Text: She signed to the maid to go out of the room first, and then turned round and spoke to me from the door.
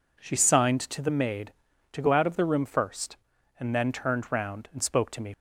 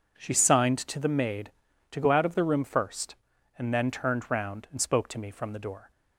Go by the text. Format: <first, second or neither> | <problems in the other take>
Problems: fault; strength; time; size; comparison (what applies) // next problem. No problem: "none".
second | stops before "from the door"; at 5.3 s